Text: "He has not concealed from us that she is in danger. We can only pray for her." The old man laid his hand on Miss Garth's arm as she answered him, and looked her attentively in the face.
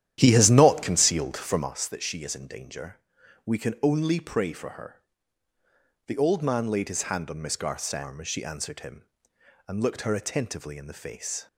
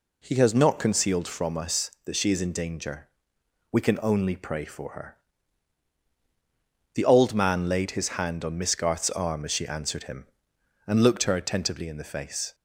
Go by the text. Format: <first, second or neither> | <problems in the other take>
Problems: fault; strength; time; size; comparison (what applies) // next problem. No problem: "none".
second | starts louder than the rest; strong; until 1.7 s; 11 dB